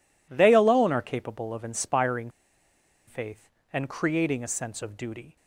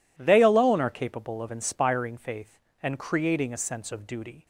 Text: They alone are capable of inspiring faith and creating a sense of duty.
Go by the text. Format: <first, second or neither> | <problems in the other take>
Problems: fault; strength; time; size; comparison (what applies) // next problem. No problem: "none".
second | pauses between "inspiring" and "faith"; noticeable; at 2.3 s; 0.76 s long